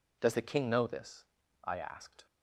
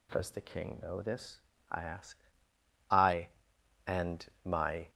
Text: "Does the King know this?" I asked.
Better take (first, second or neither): first